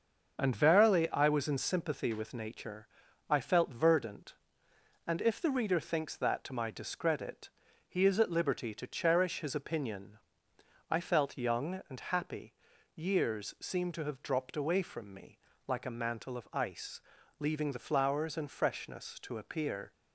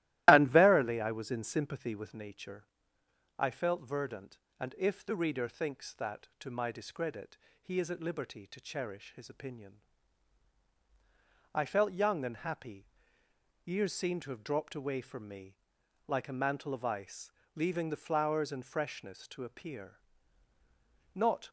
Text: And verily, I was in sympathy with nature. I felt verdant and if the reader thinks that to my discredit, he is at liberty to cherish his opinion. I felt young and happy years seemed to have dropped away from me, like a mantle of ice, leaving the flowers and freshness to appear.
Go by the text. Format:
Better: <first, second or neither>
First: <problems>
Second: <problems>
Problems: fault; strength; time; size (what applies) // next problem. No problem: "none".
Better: first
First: starts louder than the rest; until 1.4 s; 6.5 dB // pauses between "happy" and "years"; at 12.5 s; 0.42 s long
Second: starts louder than the rest; strong; until 1.3 s; 15 dB // pauses between "happy" and "years"; noticeable; at 12.8 s; 0.80 s long // goes on to say "Not"; slight; from 21.1 s on; 0.34 s long